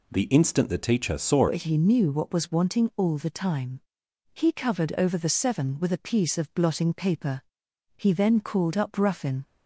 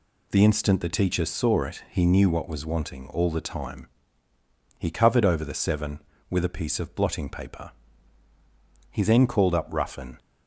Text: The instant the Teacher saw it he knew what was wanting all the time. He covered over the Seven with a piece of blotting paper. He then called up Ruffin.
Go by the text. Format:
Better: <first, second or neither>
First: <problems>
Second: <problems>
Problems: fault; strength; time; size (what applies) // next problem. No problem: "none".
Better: second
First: changes voice at "it"; from 1.4 s on; 8.0 s long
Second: none